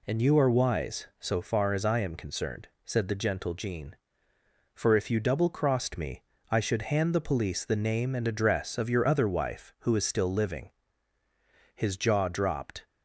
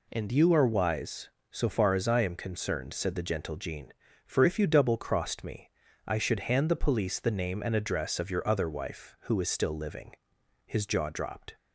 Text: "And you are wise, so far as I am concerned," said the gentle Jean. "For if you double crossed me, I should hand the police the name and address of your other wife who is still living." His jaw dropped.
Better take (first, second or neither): neither